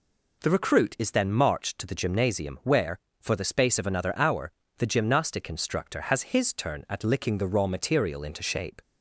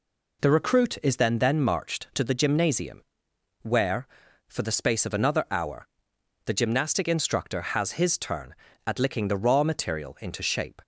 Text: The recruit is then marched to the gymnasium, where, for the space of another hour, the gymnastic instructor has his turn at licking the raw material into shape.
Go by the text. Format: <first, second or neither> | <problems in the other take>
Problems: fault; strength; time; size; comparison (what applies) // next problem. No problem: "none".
first | says "then" twice; at 1.3 s